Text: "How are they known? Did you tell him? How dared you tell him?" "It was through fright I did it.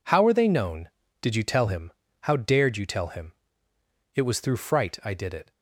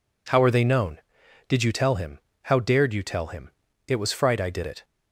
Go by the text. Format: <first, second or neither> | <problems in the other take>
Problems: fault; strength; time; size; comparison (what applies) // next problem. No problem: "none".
first | skips "through"; at 4.1 s